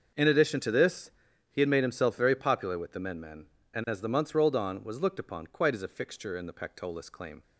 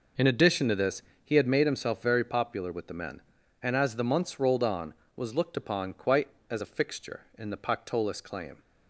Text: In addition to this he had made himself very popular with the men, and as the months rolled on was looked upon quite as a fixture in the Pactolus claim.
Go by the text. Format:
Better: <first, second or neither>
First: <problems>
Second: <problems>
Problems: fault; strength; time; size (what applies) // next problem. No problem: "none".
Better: second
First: starts louder than the rest; until 1.5 s; 6.5 dB // pauses between "this" and "he"; at 1.1 s; 0.38 s long // says "men" twice; at 3.1 s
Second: pauses between "this" and "he"; slight; at 1.0 s; 0.20 s long